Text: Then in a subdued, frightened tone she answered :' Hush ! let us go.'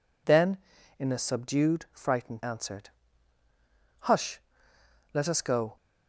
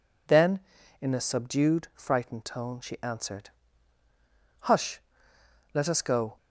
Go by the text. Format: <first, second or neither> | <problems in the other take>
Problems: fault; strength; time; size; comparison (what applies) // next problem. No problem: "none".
second | skips "tone she"; at 2.4 s